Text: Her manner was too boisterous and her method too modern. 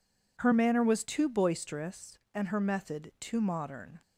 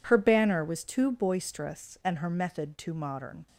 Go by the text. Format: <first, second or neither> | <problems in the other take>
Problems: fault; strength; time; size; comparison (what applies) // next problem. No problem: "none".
first | says "banner" for "manner"; at 0.1 s